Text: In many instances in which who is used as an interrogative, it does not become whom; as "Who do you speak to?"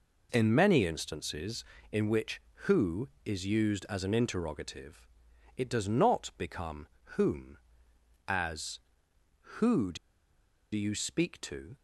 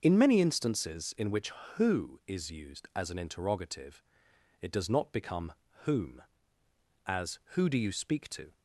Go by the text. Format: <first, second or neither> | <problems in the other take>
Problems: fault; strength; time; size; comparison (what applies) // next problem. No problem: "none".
second | pauses between "become" and "whom"; slight; at 6.8 s; 0.30 s long; slight in the second // pauses between "do" and "you"; noticeable; at 9.9 s; 0.77 s long